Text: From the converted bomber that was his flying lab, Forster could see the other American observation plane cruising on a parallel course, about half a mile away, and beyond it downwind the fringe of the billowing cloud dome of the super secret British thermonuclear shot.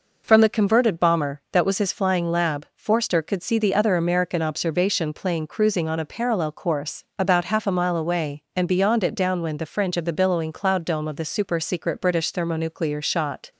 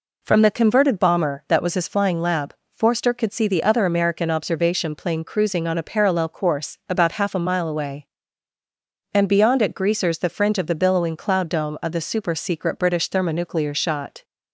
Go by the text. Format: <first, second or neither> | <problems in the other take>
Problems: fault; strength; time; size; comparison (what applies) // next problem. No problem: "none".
first | says "greasers" for "downwind"; at 9.7 s